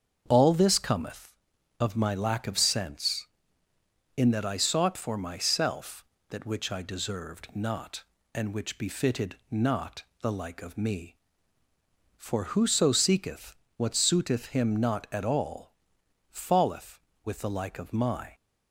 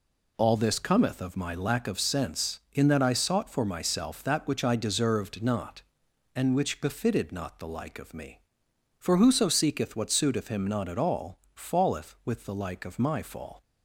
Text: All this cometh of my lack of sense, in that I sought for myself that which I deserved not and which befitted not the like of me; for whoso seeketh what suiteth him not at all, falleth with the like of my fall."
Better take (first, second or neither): second